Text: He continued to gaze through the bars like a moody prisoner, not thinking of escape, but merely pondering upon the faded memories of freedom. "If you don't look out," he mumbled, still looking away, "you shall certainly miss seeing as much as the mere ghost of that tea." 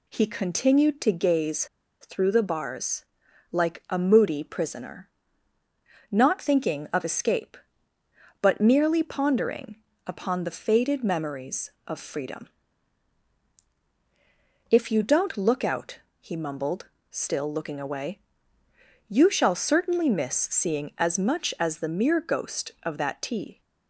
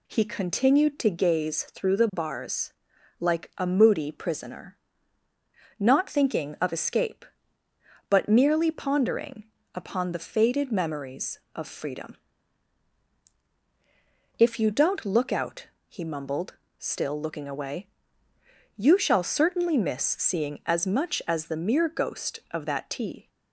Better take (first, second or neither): second